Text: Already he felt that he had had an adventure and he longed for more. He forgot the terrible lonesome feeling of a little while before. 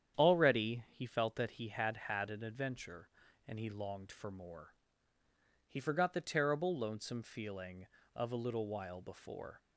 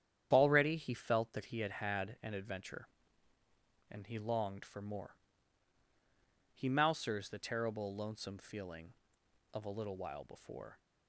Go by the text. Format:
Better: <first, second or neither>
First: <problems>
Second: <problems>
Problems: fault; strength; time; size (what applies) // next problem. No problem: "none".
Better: first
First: starts louder than the rest; strong; until 1.2 s; 9 dB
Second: starts louder than the rest; strong; until 1.3 s; 9.5 dB // says "mousers" for "forgot"; at 6.6 s